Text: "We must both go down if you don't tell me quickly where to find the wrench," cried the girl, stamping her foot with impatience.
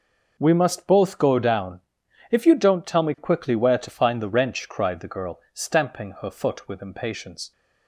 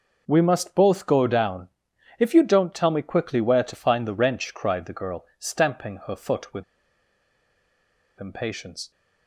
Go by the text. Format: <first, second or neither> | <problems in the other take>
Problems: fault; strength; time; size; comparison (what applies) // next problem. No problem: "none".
first | pauses between "down" and "if"; noticeable; at 1.6 s; 0.50 s long; noticeable in the first // pauses between "with" and "impatience"; strong; at 6.6 s; 1.5 s long